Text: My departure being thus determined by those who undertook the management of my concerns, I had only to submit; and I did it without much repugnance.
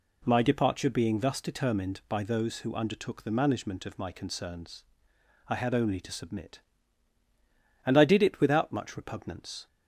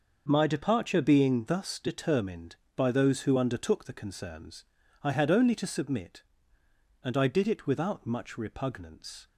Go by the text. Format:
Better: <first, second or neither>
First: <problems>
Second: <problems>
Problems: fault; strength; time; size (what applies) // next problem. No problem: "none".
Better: first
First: none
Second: starts louder than the rest; noticeable; until 1.2 s; 6 dB // skips "management of my"; at 3.9 s